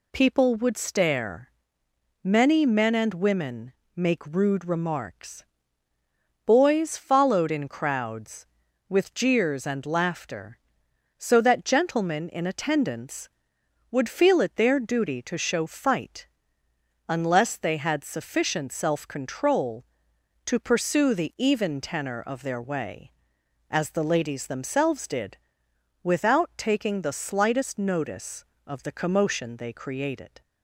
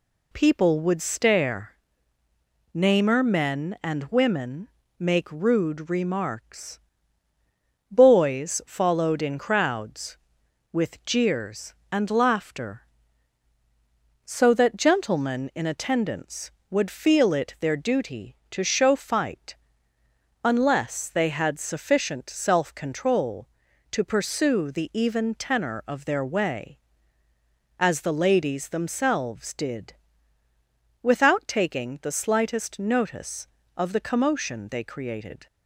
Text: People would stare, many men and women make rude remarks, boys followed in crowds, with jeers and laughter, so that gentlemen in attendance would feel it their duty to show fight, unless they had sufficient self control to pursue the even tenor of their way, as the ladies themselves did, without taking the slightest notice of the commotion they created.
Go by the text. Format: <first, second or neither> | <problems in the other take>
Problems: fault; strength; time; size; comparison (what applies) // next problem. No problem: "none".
first | says "namer" for "many"; at 2.7 s // pauses between "women" and "make"; slight; at 4.6 s; 0.28 s long; slight in the first